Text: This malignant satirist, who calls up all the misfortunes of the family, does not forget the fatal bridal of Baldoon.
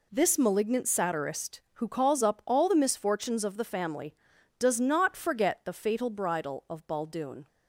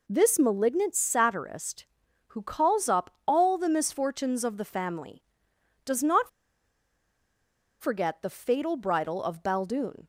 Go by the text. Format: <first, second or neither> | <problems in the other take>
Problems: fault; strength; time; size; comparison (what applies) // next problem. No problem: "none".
first | pauses between "up" and "all"; slight; at 3.1 s; 0.16 s long // pauses between "not" and "forget"; strong; at 6.2 s; 1.5 s long